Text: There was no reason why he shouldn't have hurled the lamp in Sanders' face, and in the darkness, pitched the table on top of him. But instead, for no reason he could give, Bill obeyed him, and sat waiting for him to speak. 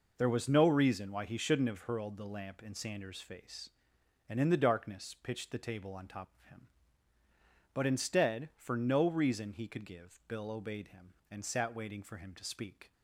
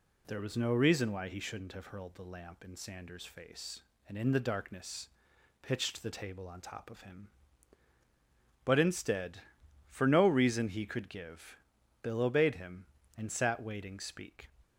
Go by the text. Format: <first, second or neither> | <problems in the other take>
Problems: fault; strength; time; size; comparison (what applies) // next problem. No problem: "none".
first | skips "for him to"; at 13.9 s